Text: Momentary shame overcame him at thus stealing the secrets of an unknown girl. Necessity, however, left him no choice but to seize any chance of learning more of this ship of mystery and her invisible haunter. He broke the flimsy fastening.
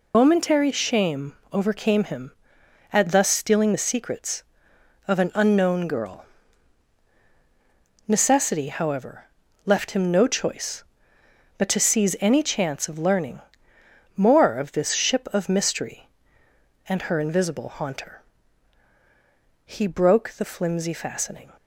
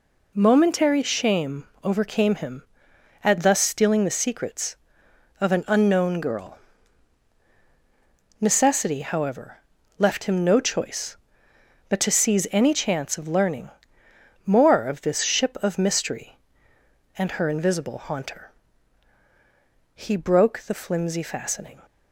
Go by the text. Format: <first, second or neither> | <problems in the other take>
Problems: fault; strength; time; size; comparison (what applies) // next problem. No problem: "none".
second | loses the start of "Momentary"; at 0.1 s; 115 ms // pauses between "shame" and "overcame"; slight; at 1.3 s; 0.18 s long; slight in the second // pauses between "learning" and "more"; noticeable; at 13.4 s; 0.74 s long; noticeable in the second